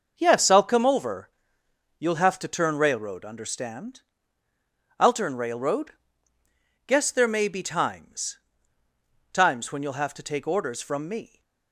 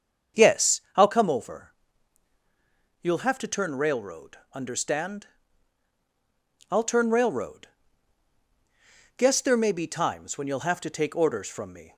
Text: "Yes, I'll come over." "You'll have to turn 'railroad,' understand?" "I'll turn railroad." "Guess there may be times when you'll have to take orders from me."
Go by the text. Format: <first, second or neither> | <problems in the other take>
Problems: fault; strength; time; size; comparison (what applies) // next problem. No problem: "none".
second | starts louder than the rest; noticeable; until 1.1 s; 6 dB; also in the second // says "times" twice; at 9.3 s